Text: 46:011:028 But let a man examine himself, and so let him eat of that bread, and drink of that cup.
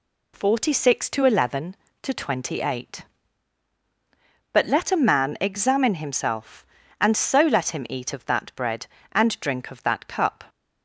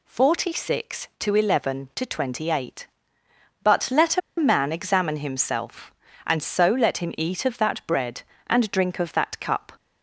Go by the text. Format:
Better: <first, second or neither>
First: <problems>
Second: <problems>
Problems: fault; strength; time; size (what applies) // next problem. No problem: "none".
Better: first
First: none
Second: pauses between "a" and "man"; slight; at 4.2 s; 0.19 s long